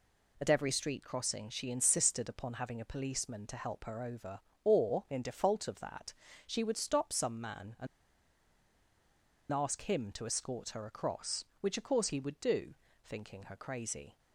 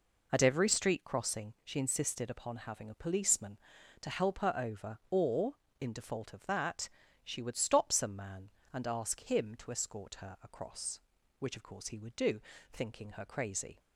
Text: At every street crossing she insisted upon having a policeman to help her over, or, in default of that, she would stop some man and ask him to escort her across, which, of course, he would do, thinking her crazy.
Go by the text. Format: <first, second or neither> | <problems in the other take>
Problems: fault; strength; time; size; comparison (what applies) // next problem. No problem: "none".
second | pauses between "and" and "ask"; strong; at 7.8 s; 1.6 s long